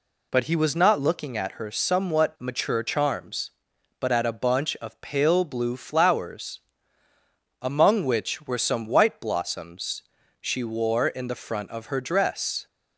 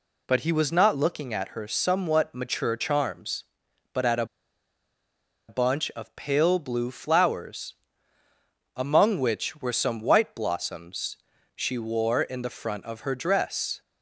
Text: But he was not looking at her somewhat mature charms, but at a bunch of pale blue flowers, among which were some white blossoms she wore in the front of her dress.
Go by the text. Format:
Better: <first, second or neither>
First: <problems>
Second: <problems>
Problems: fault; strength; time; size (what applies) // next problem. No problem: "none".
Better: first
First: pauses between "blossoms" and "she"; at 10.0 s; 0.38 s long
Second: pauses between "a" and "bunch"; at 4.2 s; 1.2 s long // pauses between "blossoms" and "she"; at 11.1 s; 0.38 s long